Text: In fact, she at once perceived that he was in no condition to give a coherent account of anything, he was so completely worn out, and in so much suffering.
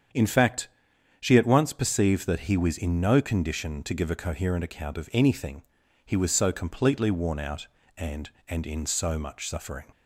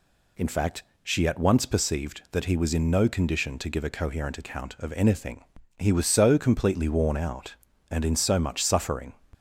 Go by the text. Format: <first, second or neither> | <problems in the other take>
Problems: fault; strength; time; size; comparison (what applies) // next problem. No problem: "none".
second | starts louder than the rest; strong; until 1.6 s; 8 dB // says "and" twice; at 8.4 s